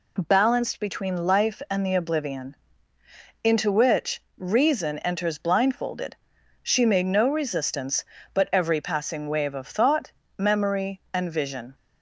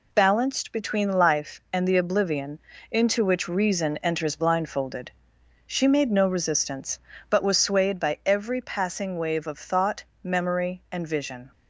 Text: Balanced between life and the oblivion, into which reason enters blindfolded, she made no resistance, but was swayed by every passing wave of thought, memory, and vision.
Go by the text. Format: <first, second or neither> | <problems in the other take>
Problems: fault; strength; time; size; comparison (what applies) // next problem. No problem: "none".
second | pauses between "which" and "reason"; slight; at 4.2 s; 0.16 s long // skips "was swayed by"; at 8.4 s